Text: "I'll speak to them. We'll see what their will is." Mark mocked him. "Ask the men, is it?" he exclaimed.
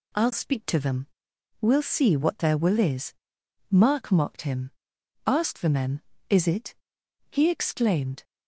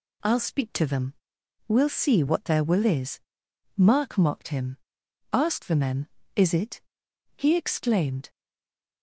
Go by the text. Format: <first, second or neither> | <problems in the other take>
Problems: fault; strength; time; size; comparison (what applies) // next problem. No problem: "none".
first | stays silent after the last word; slight; from 8.2 s on; 0.8 s long